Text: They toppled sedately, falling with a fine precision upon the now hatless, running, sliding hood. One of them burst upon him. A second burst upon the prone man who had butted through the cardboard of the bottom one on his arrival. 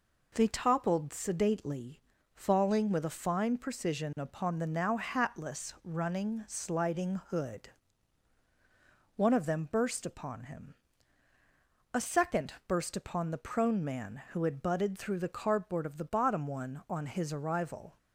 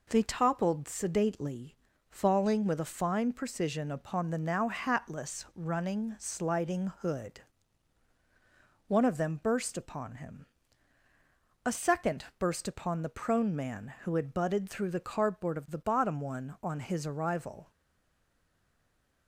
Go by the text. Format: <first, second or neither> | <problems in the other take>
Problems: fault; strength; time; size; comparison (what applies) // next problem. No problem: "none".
first | stays silent after the last word; noticeable; from 17.7 s on; 1.5 s long